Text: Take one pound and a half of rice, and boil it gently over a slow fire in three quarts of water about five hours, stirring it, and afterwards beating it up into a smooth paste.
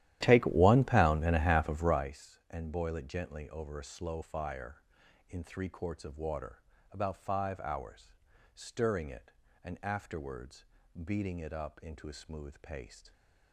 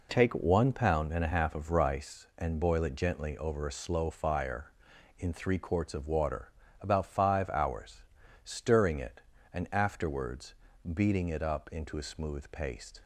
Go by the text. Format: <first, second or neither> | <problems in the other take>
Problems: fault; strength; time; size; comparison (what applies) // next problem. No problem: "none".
second | starts louder than the rest; strong; until 2.1 s; 13 dB // pauses between "water" and "about"; slight; at 6.6 s; 0.30 s long; slight in the second // pauses between "afterwards" and "beating"; at 10.6 s; 0.40 s long; also in the second